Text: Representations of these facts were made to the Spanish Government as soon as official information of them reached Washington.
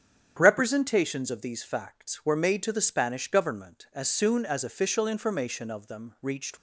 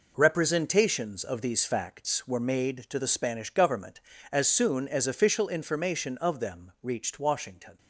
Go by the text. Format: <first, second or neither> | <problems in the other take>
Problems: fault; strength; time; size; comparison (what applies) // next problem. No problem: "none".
second | starts louder than the rest; strong; until 1.4 s; 9 dB // stops before "Washington"; at 6.5 s